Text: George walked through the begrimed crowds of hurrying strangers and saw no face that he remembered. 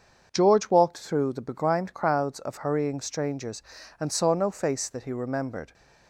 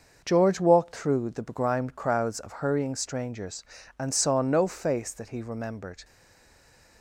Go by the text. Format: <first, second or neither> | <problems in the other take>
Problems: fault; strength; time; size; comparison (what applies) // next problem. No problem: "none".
first | starts louder than the rest; until 1.2 s; 6.5 dB; also in the first // stays silent after the last word; slight; from 6.0 s on; 1.0 s long